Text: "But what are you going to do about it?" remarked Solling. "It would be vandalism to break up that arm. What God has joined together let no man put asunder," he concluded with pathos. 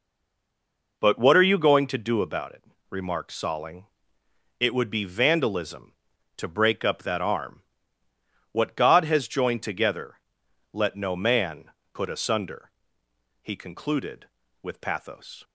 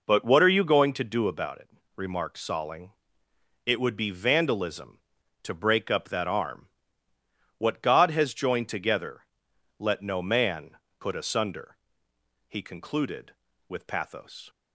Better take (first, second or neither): second